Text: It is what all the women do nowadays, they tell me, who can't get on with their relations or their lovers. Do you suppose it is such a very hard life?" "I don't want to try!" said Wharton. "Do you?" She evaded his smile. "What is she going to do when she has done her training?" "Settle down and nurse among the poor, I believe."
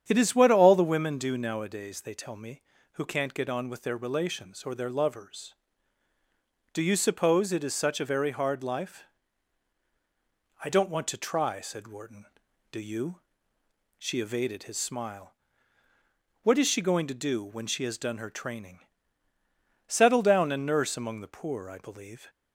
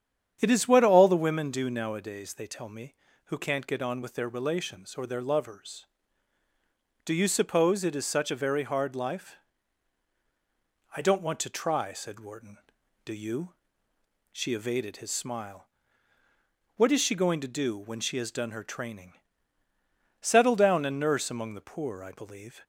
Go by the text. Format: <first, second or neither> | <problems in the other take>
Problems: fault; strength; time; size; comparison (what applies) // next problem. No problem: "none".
neither | starts louder than the rest; strong; the same in both